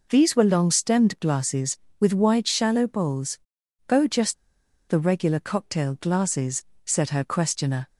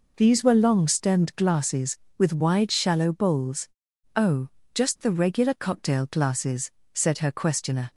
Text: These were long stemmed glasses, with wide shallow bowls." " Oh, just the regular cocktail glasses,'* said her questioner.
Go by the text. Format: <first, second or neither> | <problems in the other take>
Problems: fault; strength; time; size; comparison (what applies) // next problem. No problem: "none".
second | pauses between "just" and "the"; noticeable; at 4.3 s; 0.54 s long